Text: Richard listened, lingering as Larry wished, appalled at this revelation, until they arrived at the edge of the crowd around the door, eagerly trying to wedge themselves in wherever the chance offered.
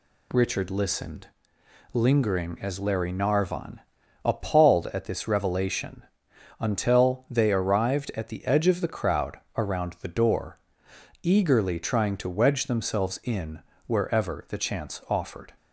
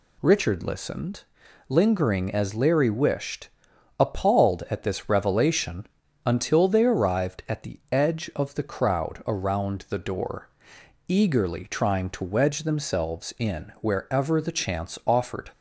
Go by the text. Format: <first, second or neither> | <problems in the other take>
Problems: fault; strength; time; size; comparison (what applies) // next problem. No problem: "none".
second | says "narvon" for "wished"; at 3.1 s // pauses between "crowd" and "around"; slight; at 9.3 s; 0.20 s long // pauses between "in" and "wherever"; slight; at 13.5 s; 0.26 s long